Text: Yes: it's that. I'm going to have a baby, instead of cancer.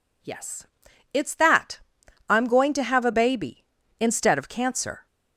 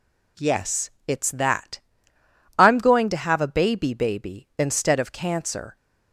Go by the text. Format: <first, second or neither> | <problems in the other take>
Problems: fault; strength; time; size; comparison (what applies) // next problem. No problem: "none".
first | says "baby" twice; at 3.9 s